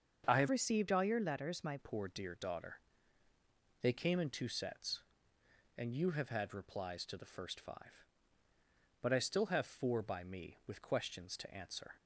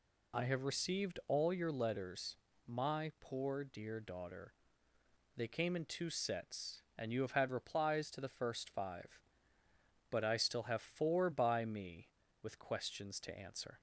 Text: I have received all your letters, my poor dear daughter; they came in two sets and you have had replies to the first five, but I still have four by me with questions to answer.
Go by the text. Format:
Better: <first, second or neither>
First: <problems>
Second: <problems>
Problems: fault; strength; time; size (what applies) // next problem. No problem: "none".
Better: second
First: starts louder than the rest; until 1.2 s; 7 dB // changes voice from "received" to "my"; from 0.5 to 1.7 s; 1.2 s long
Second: none